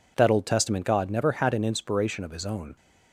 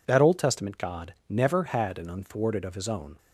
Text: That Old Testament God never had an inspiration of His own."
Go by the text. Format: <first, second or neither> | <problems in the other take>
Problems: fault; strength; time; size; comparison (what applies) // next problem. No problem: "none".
first | says "unthwarted" for "inspiration"; at 2.0 s